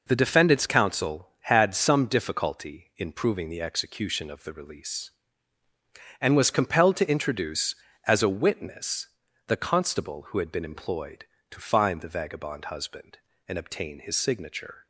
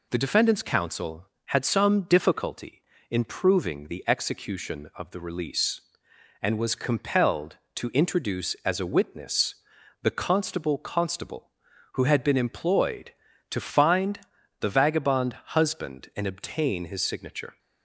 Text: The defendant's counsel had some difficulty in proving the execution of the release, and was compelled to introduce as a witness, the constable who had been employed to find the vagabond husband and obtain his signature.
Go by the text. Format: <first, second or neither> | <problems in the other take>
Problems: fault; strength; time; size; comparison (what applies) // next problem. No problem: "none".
first | says "constable" twice; at 10.7 s // pauses between "find" and "the"; at 14.2 s; 0.40 s long